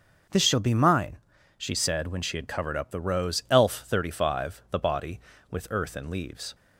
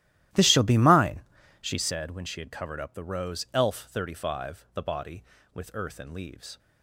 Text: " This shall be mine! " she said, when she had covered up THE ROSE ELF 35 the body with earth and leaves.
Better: first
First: none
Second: starts louder than the rest; strong; until 2.0 s; 12.5 dB

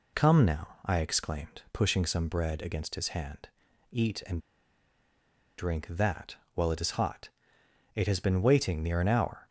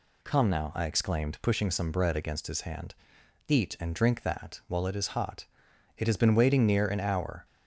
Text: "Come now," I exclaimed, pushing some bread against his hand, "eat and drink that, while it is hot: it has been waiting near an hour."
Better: second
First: pauses between "and" and "drink"; at 4.3 s; 1.1 s long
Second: none

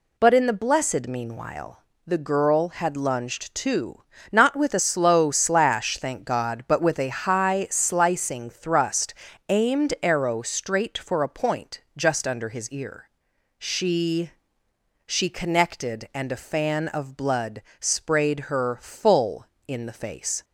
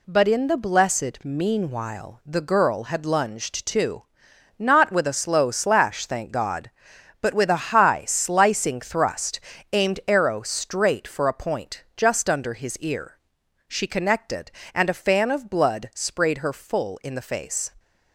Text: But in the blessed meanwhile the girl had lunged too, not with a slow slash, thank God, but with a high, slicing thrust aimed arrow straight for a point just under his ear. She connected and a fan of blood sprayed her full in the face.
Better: second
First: pauses between "meanwhile" and "the"; slight; at 1.8 s; 0.26 s long // pauses between "thrust" and "aimed"; slight; at 9.1 s; 0.34 s long // pauses between "point" and "just"; slight; at 11.7 s; 0.16 s long // says "She" twice; at 15.0 s // pauses between "blood" and "sprayed"; slight; at 17.6 s; 0.18 s long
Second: pauses between "thrust" and "aimed"; slight; at 9.3 s; 0.34 s long

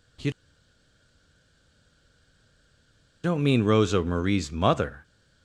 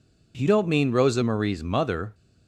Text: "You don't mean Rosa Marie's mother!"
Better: second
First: pauses between "You" and "don't"; strong; at 0.3 s; 2.9 s long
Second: none

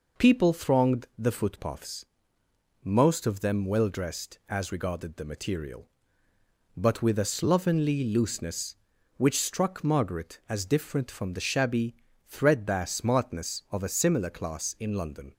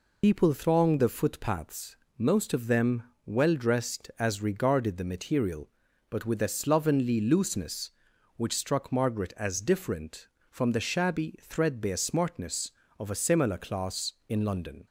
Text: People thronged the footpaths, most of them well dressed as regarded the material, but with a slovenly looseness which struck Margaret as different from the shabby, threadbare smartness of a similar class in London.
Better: first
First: none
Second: loses the start of "People"; at 0.2 s; 65 ms // pauses between "them" and "well"; slight; at 3.0 s; 0.23 s long

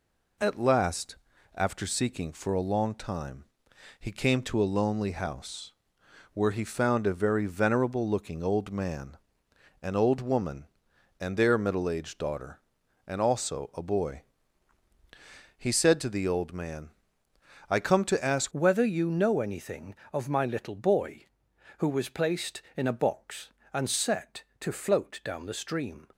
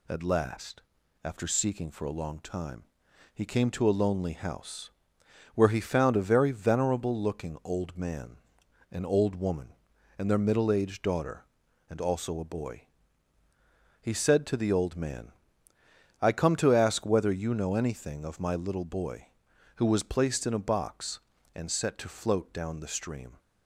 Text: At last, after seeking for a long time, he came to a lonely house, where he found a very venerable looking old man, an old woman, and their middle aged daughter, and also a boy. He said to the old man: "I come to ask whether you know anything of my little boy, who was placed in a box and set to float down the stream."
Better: second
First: changes voice at "whether"; from 18.5 s on; 7.5 s long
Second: none

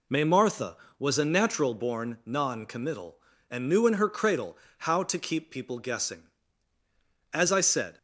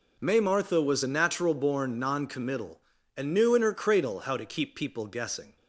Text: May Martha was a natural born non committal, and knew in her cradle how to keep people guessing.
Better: second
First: pauses between "cradle" and "how"; slight; at 4.5 s; 0.22 s long // goes on to say "As I said"; noticeable; from 7.3 s on; 0.64 s long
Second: none

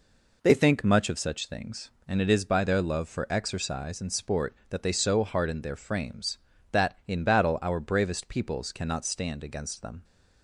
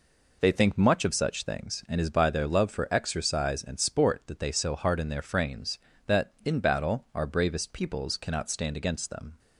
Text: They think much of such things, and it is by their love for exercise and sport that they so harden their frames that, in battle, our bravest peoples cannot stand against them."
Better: first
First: none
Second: skips "it"; at 1.9 s

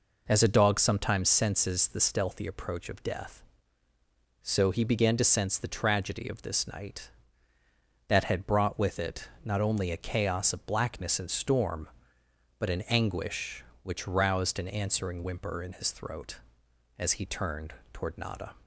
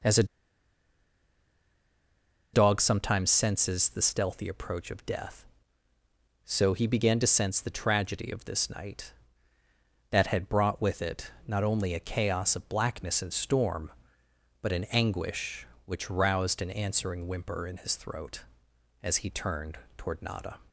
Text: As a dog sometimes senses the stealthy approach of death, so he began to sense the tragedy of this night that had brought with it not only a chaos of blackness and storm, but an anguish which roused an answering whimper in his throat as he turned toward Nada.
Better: first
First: pauses between "it" and "not"; slight; at 9.2 s; 0.16 s long // pauses between "turned" and "toward"; slight; at 17.7 s; 0.18 s long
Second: pauses between "a" and "dog"; strong; at 0.2 s; 2.2 s long // pauses between "it" and "not"; slight; at 11.3 s; 0.16 s long // pauses between "turned" and "toward"; slight; at 19.7 s; 0.18 s long

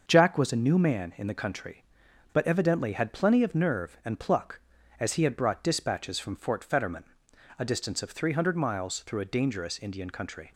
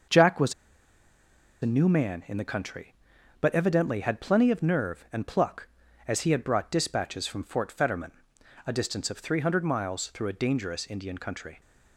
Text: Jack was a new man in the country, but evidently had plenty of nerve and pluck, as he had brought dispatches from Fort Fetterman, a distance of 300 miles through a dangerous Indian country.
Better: first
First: starts louder than the rest; until 1.0 s; 6.5 dB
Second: starts louder than the rest; until 2.1 s; 6.5 dB // pauses between "was" and "a"; at 0.5 s; 1.0 s long

